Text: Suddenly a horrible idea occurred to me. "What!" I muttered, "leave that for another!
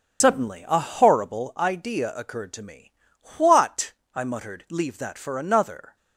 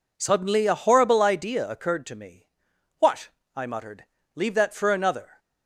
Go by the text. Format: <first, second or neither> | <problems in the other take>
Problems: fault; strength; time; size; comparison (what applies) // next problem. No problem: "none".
second | loses the start of "Suddenly"; at 0.2 s; 75 ms